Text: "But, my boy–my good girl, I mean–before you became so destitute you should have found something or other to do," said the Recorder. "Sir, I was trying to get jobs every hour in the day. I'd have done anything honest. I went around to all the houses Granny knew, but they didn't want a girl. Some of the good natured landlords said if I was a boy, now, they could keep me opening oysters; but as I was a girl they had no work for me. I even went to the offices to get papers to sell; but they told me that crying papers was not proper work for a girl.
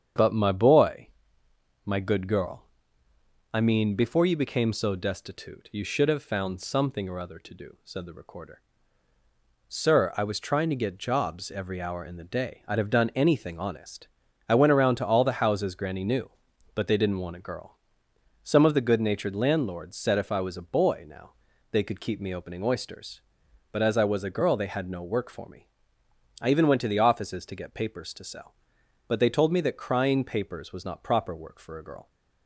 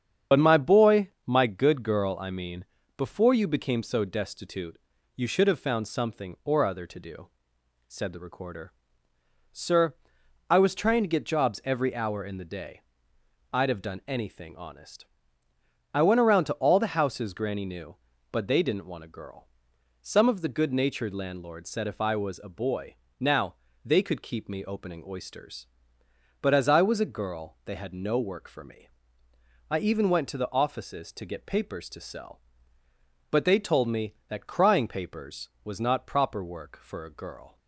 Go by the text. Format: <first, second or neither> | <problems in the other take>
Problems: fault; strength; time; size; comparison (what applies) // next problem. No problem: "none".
first | loses the start of "But"; at 0.3 s; 55 ms // starts louder than the rest; strong; until 1.4 s; 8 dB; strong in the first // pauses between "destitute" and "you"; at 4.7 s; 0.38 s long